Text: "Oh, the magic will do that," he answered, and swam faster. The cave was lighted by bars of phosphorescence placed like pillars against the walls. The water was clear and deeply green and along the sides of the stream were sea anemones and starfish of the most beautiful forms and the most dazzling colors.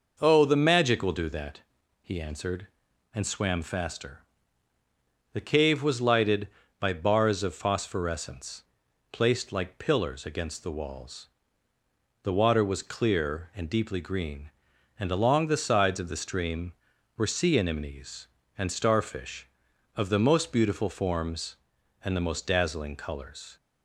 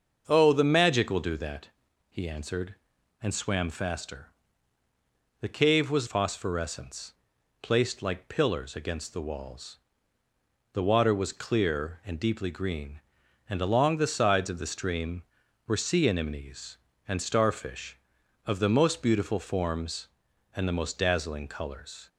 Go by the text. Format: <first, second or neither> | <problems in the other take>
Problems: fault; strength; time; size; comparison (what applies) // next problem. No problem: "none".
first | starts louder than the rest; until 1.2 s; 6.5 dB // skips "lighted by bars of"; at 6.0 s // pauses between "phosphorescence" and "placed"; noticeable; at 7.1 s; 0.48 s long; noticeable in the first